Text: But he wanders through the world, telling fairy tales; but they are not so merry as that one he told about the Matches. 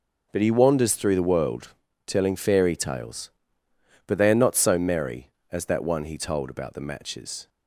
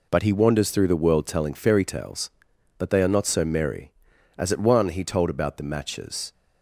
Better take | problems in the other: first | says "at" for "that"; at 4.5 s

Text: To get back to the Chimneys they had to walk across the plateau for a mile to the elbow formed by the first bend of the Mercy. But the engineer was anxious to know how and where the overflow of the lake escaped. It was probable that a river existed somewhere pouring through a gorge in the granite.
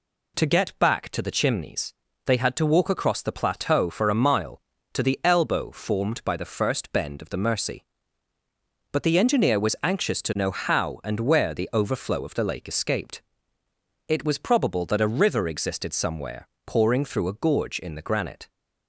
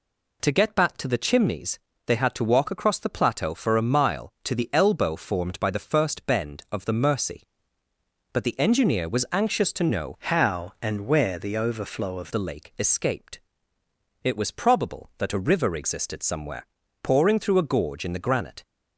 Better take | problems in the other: first | pauses between "Chimneys" and "they"; slight; at 1.7 s; 0.28 s long; slight in the first // changes voice from "how" to "of"; from 10.1 to 12.2 s; 2.1 s long // pauses between "somewhere" and "pouring"; at 16.6 s; 0.38 s long; slight in the first

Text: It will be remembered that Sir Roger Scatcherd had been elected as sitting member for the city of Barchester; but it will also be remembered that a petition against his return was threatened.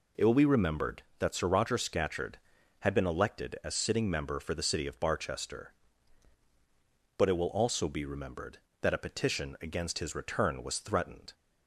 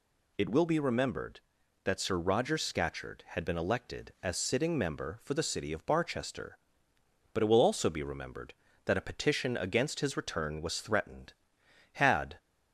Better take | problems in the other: first | goes on to say "Had"; slight; from 11.9 s on; 0.46 s long

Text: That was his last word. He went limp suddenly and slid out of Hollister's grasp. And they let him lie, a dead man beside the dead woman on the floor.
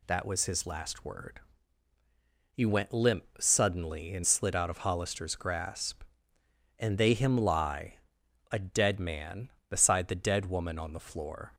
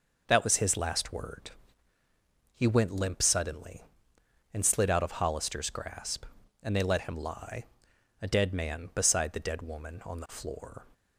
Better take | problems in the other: second | pauses between "limp" and "suddenly"; slight; at 3.2 s; 0.16 s long // skips "let"; at 7.1 s

